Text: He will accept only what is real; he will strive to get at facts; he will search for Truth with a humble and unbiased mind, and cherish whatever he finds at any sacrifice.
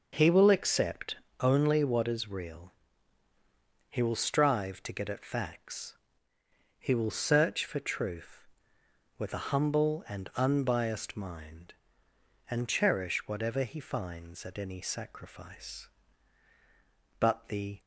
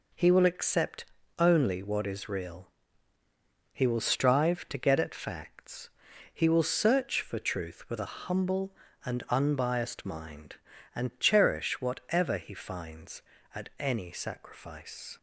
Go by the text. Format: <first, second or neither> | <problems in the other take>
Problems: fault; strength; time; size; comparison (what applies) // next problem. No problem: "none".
second | pauses between "accept" and "only"; slight; at 1.1 s; 0.24 s long; slight in the second // goes on to say "But the"; noticeable; from 17.1 s on; 0.62 s long